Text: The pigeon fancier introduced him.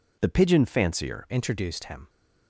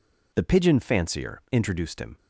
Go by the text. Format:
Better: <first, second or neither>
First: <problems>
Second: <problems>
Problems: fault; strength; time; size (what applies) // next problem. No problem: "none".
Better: second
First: changes voice at "introduced"; from 1.2 s on; 0.8 s long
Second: none